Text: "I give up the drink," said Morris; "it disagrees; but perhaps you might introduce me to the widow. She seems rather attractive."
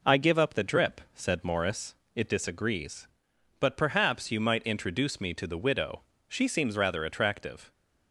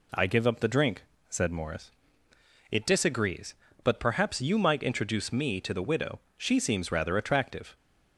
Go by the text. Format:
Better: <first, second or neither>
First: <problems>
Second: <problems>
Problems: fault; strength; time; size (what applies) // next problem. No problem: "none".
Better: second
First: says "drip" for "drink"; at 0.6 s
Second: none